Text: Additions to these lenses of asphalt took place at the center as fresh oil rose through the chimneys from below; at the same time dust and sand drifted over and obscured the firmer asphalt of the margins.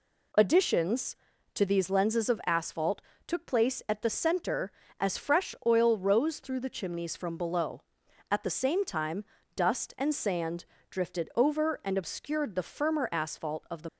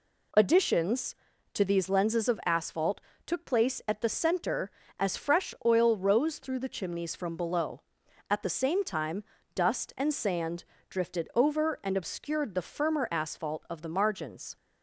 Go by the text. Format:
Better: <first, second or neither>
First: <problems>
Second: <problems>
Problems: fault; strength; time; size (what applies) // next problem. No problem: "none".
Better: second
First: pauses between "asphalt" and "took"; slight; at 3.0 s; 0.26 s long // pauses between "time" and "dust"; slight; at 9.2 s; 0.32 s long // pauses between "sand" and "drifted"; slight; at 10.6 s; 0.26 s long // stops before "margins"; at 13.8 s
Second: pauses between "asphalt" and "took"; slight; at 3.0 s; 0.26 s long // pauses between "time" and "dust"; slight; at 9.2 s; 0.32 s long // pauses between "sand" and "drifted"; slight; at 10.6 s; 0.26 s long